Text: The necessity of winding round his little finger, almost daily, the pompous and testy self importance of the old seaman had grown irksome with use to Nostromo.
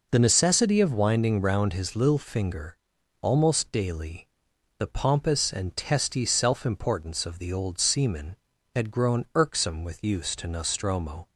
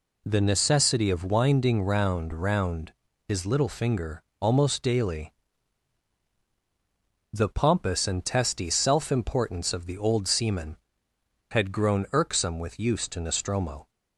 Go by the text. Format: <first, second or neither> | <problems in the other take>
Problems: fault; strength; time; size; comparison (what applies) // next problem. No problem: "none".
first | says "round" twice; at 2.3 s